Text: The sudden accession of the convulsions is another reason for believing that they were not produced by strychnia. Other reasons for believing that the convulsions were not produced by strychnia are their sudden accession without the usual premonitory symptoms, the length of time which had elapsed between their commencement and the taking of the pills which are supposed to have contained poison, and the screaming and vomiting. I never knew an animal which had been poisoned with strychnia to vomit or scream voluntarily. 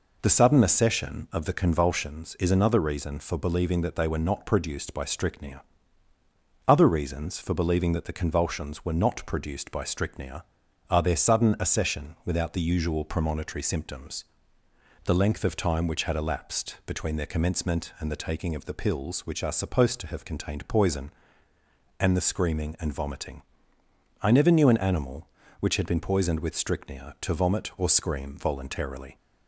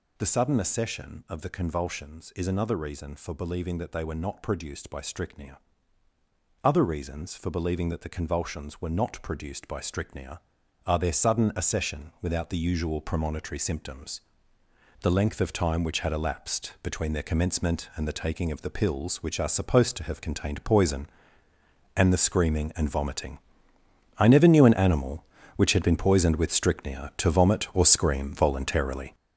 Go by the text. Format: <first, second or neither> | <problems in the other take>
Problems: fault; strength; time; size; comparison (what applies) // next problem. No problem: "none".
first | gets louder; strong; throughout; 8 dB